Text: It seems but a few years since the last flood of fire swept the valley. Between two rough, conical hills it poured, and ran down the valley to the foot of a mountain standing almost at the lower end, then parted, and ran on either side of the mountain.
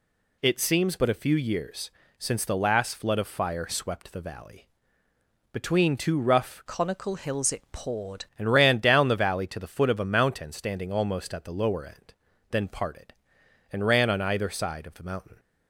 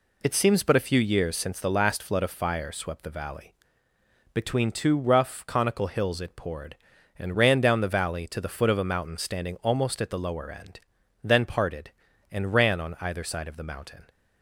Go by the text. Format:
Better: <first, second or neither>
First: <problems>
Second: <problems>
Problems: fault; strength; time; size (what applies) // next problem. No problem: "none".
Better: second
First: pauses between "years" and "since"; slight; at 1.9 s; 0.30 s long // changes voice from "conical" to "poured"; from 6.6 to 8.2 s; 1.6 s long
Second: none